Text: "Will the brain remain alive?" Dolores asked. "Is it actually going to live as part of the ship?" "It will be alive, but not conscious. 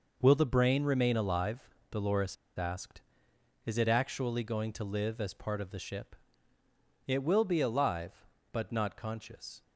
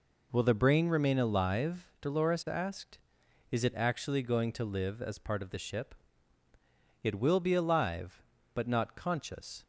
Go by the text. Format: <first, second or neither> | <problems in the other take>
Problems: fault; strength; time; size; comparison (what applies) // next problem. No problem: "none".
second | pauses between "Dolores" and "asked"; slight; at 2.3 s; 0.22 s long